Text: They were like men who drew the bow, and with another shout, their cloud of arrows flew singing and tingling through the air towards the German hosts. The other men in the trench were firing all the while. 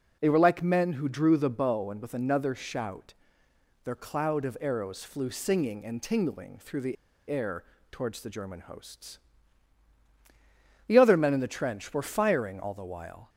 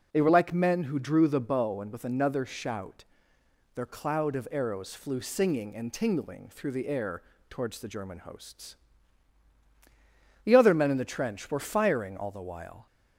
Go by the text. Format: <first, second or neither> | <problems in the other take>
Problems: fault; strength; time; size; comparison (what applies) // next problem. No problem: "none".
second | pauses between "the" and "air"; slight; at 6.9 s; 0.33 s long // pauses between "air" and "towards"; slight; at 7.6 s; 0.28 s long; slight in the second